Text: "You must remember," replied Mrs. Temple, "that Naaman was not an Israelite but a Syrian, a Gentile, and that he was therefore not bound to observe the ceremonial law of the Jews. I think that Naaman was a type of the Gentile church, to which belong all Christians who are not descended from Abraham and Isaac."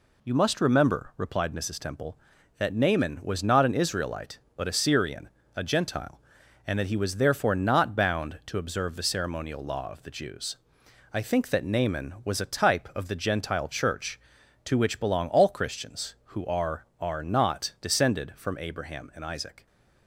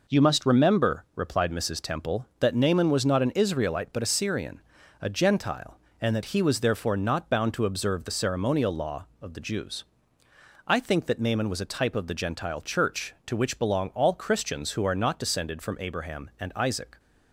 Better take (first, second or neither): second